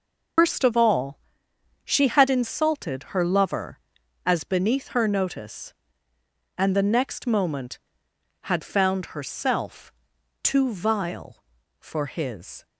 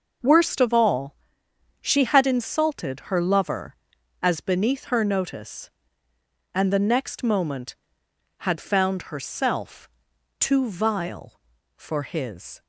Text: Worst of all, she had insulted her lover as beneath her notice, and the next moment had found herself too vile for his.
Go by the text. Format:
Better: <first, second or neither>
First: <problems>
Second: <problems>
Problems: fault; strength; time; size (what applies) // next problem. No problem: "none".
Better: second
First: loses the start of "Worst"; at 0.3 s; 130 ms // pauses between "herself" and "too"; noticeable; at 9.9 s; 0.50 s long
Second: pauses between "herself" and "too"; noticeable; at 9.8 s; 0.50 s long